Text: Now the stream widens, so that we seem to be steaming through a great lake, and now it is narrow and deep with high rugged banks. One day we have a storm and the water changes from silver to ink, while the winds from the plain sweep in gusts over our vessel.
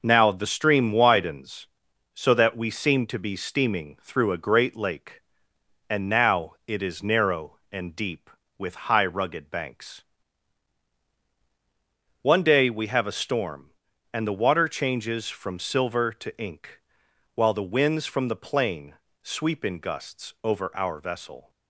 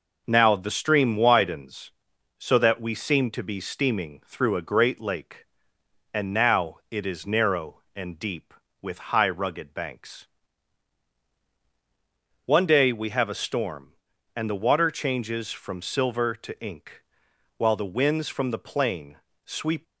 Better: first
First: pauses between "now" and "it"; slight; at 6.5 s; 0.16 s long // pauses between "plain" and "sweep"; slight; at 18.9 s; 0.28 s long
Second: pauses between "now" and "it"; slight; at 6.7 s; 0.15 s long // pauses between "plain" and "sweep"; slight; at 19.1 s; 0.28 s long // stops before "in gusts over our vessel"; at 19.8 s

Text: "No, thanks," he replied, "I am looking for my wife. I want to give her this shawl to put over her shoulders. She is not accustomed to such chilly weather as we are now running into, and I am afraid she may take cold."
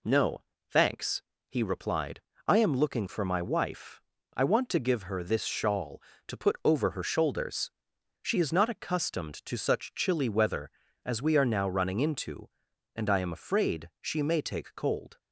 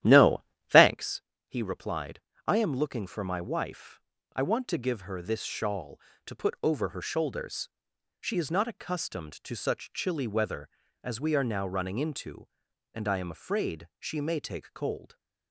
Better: first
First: none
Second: starts louder than the rest; strong; until 1.0 s; 12 dB

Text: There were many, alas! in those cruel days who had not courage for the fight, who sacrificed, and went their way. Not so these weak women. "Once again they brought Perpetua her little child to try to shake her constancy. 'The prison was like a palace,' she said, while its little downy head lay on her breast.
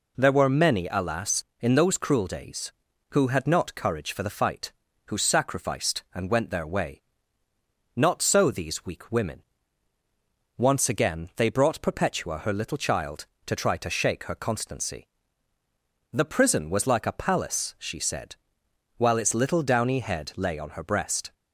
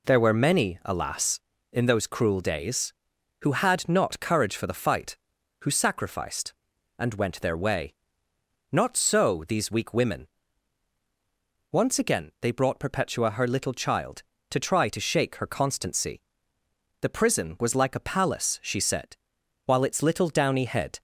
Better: first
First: none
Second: stops before "lay on her breast"; at 20.9 s

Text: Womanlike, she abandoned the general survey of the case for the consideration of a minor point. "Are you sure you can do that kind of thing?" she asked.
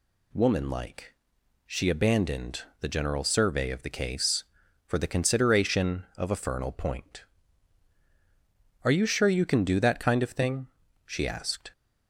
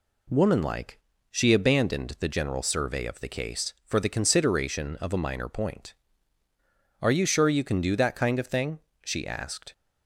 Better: second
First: pauses between "abandoned" and "the"; slight; at 2.6 s; 0.18 s long // says "fernal" for "minor"; at 6.3 s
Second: none

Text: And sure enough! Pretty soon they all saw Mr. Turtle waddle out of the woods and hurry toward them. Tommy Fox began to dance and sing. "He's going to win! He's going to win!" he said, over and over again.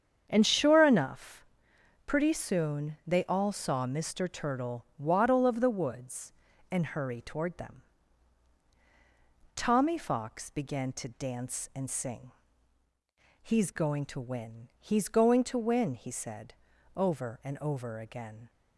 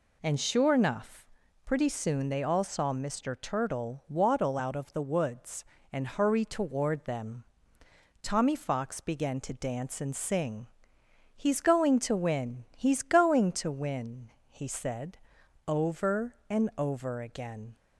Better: second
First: starts louder than the rest; strong; until 1.2 s; 8 dB // skips "out"; at 5.4 s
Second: none

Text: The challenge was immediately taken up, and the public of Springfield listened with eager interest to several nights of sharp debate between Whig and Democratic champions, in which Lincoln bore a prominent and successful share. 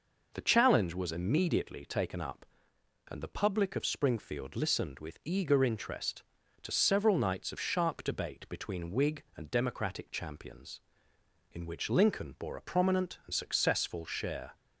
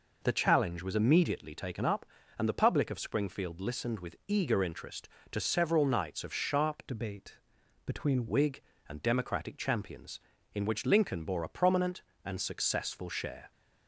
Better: first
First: none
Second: changes voice from "debate" to "between"; from 6.8 to 8.2 s; 1.4 s long // pauses between "debate" and "between"; noticeable; at 7.3 s; 0.48 s long

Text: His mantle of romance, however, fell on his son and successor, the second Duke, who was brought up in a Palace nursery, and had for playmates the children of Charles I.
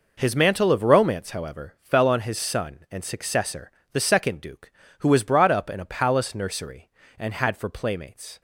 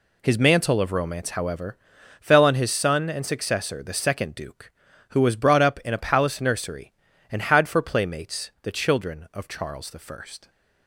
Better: second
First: stops before "the children of Charles I"; at 8.3 s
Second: none

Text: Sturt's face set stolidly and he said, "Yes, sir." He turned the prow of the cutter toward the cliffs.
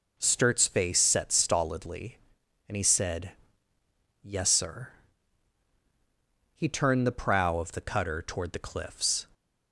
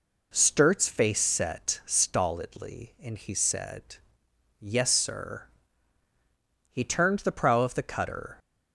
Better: first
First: none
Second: stops before "toward the cliffs"; at 8.3 s

